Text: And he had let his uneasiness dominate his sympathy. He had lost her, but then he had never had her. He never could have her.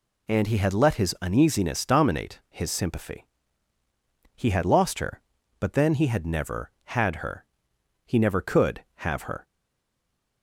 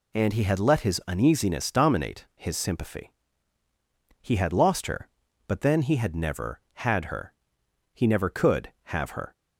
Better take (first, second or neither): second